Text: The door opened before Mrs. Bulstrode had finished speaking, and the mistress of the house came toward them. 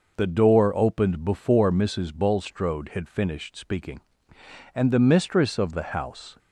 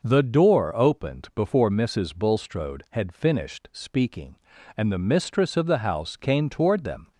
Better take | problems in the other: second | stops before "came toward them"; at 6.3 s

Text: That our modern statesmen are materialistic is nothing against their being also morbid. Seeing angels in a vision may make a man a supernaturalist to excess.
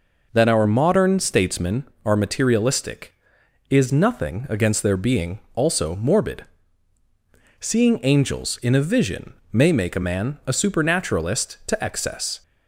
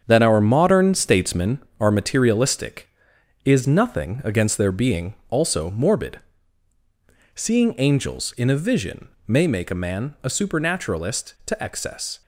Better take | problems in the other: first | gets quieter; strong; throughout; 8 dB // pauses between "being" and "also"; slight; at 5.1 s; 0.16 s long; slight in the first // pauses between "vision" and "may"; slight; at 9.0 s; 0.20 s long; slight in the first

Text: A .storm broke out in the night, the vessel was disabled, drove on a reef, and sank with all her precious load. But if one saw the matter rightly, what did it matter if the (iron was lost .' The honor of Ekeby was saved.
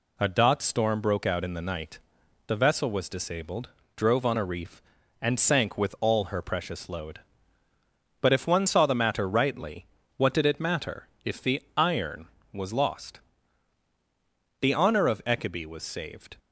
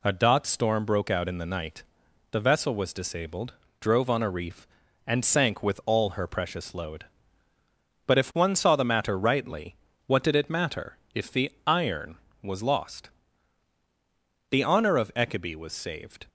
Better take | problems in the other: neither | pauses between "matter" and "if"; slight; the same in both

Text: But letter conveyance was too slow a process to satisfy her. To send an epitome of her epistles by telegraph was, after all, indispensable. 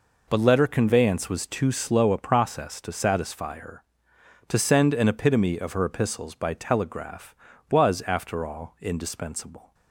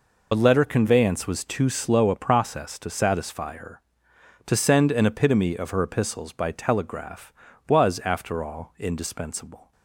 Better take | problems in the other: first | loses the start of "But"; at 0.3 s; 40 ms

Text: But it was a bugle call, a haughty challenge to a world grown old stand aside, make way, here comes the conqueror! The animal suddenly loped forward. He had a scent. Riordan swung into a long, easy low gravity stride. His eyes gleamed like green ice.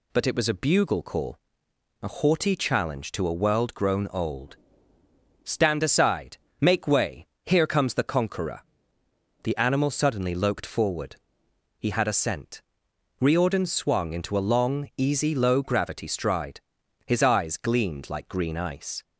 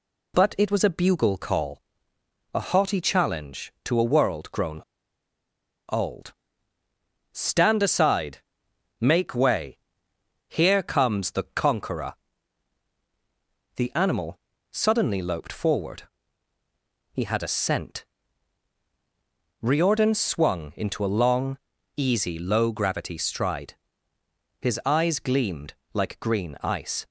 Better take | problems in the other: first | pauses between "grown" and "old"; at 4.8 s; 1.0 s long // pauses between "old" and "stand"; noticeable; at 6.3 s; 0.98 s long; noticeable in the first // pauses between "animal" and "suddenly"; slight; at 14.3 s; 0.34 s long // pauses between "gleamed" and "like"; slight; at 25.7 s; 0.22 s long

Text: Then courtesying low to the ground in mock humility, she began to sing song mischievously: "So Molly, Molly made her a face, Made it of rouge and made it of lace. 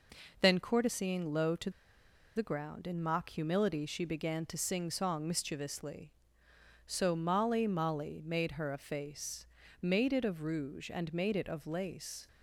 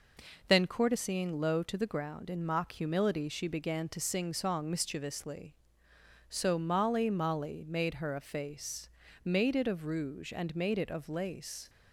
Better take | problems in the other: second | pauses between "to" and "the"; noticeable; at 1.6 s; 0.66 s long

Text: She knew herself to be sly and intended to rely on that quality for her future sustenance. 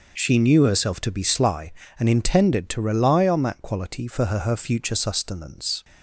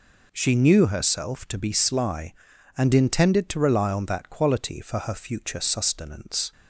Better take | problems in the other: second | says "her" twice; at 4.3 s

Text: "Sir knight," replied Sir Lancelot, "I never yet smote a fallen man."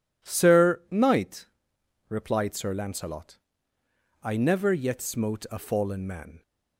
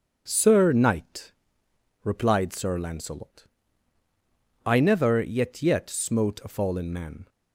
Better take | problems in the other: first | starts louder than the rest; strong; until 1.2 s; 7 dB // says "yet" twice; at 5.6 s

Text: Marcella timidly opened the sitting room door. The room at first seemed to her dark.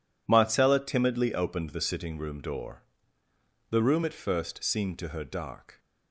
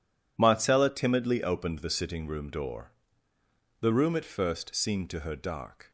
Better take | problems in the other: neither | none

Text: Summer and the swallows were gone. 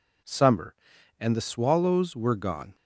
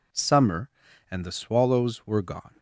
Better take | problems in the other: neither | none

